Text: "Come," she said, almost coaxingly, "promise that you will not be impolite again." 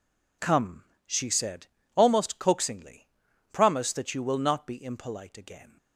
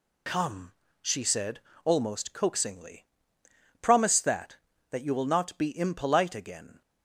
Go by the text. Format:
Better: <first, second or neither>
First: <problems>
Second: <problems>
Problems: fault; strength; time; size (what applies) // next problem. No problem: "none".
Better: first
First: none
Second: says "that" twice; at 4.8 s